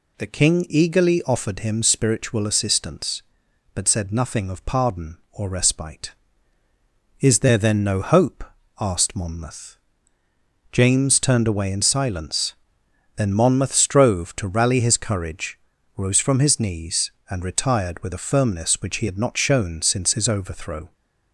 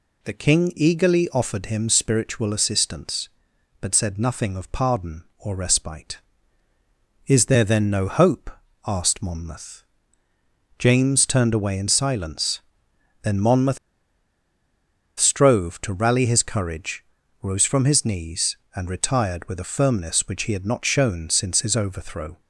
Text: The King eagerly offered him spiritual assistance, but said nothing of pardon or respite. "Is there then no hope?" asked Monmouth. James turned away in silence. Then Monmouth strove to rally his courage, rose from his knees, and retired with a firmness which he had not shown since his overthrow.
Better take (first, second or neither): first